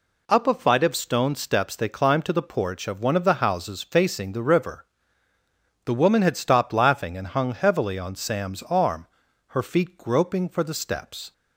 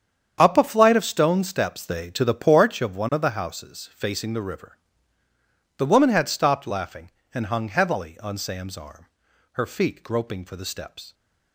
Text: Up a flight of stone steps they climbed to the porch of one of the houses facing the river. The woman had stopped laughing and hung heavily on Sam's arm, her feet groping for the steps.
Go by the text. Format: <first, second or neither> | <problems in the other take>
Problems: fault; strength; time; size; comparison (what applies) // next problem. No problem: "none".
first | starts louder than the rest; strong; until 1.4 s; 8 dB // skips "climbed"; at 2.1 s